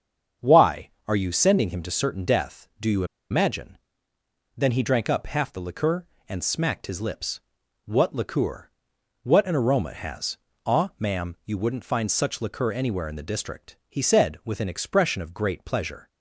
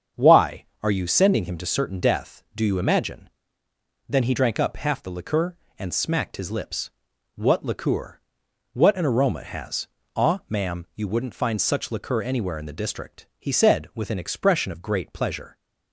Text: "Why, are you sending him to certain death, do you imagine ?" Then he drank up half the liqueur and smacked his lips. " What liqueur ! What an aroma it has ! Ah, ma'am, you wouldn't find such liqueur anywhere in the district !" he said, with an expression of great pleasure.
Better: second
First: starts louder than the rest; strong; until 1.5 s; 8 dB // pauses between "you" and "imagine"; slight; at 3.0 s; 0.26 s long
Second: starts louder than the rest; strong; until 1.3 s; 8 dB

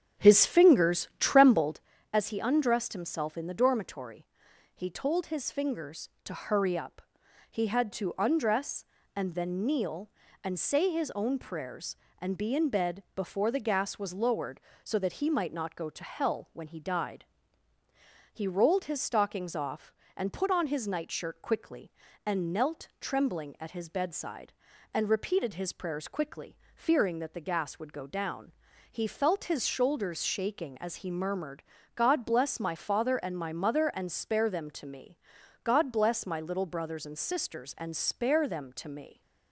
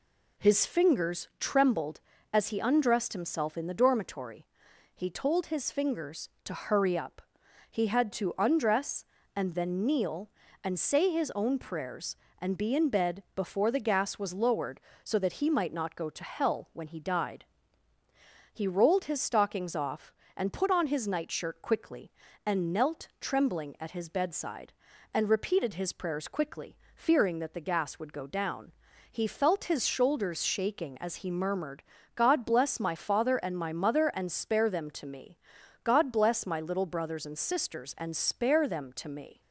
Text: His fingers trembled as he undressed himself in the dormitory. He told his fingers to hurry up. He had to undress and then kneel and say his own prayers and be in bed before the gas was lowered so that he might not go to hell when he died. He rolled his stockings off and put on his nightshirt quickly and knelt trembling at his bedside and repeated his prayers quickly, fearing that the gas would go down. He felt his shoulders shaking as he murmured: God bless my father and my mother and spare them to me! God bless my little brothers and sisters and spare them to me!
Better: second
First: starts louder than the rest; strong; until 1.9 s; 8 dB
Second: none

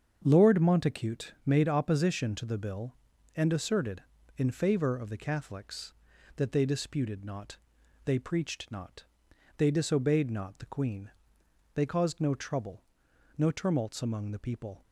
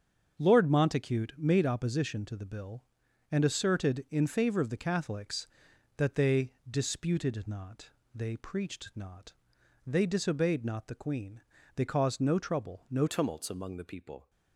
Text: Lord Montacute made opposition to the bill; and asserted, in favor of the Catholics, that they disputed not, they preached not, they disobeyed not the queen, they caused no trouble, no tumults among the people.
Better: first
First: starts louder than the rest; strong; until 1.2 s; 7 dB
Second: starts louder than the rest; strong; until 1.4 s; 7 dB // pauses between "they" and "disputed"; slight; at 6.5 s; 0.16 s long // changes voice at "tumults"; from 13.0 s on; 1.2 s long

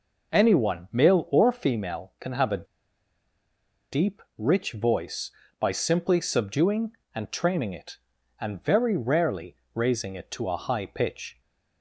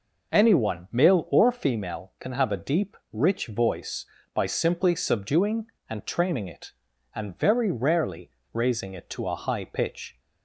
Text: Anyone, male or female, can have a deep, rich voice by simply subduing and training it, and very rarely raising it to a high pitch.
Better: second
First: pauses between "a" and "deep"; strong; at 2.6 s; 1.2 s long // pauses between "rarely" and "raising"; slight; at 9.5 s; 0.18 s long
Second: pauses between "rarely" and "raising"; slight; at 8.3 s; 0.22 s long

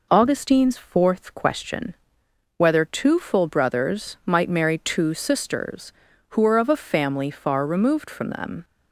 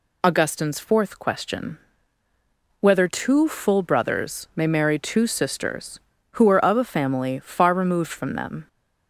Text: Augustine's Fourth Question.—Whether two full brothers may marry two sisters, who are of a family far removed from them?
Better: second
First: says "might" for "may"; at 4.2 s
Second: none

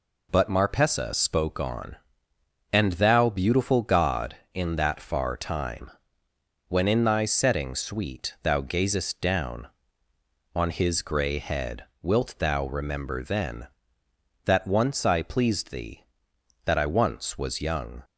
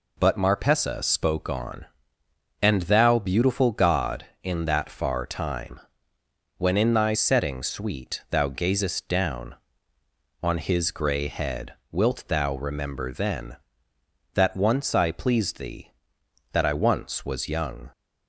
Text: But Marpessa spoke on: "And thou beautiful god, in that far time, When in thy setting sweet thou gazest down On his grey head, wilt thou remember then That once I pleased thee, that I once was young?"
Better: neither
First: none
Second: none

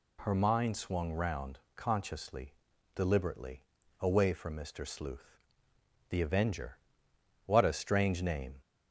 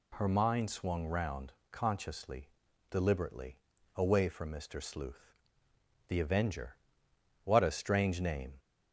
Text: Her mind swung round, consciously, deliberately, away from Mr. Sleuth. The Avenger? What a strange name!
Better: neither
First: none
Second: none

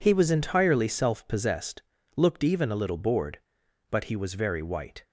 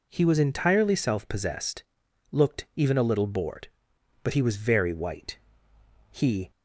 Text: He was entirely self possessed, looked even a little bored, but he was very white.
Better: first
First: none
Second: goes on to say "He"; slight; from 6.0 s on; 0.40 s long

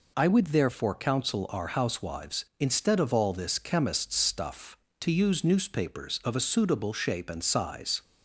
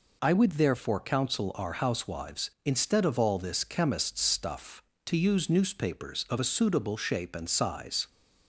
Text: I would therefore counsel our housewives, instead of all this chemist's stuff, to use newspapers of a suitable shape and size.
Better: neither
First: none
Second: none

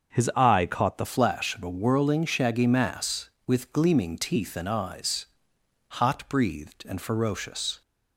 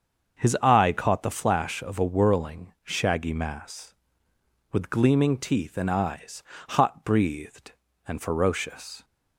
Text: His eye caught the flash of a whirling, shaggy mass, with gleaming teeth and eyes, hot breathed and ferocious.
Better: second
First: starts louder than the rest; until 1.1 s; 6.5 dB // changes voice at "flash"; from 1.0 s on; 6.8 s long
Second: starts louder than the rest; until 1.4 s; 7 dB

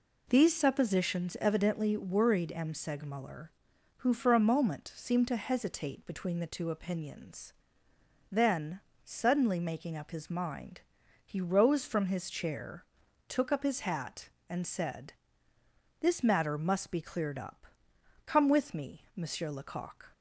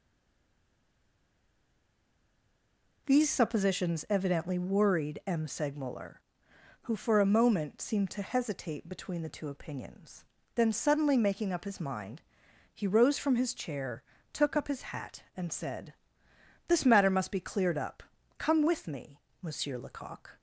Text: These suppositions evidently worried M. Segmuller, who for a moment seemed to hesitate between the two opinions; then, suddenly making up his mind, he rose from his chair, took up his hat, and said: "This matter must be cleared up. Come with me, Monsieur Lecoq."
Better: first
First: none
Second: stays silent before the first word; strong; until 3.0 s; 3.0 s long

